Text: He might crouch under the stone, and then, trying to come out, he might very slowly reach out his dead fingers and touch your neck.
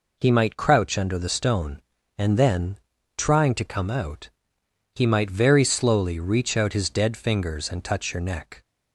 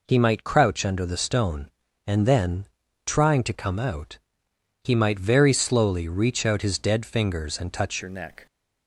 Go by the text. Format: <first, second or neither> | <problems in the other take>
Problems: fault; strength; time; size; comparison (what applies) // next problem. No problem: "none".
first | changes voice at "your"; from 8.0 s on; 0.4 s long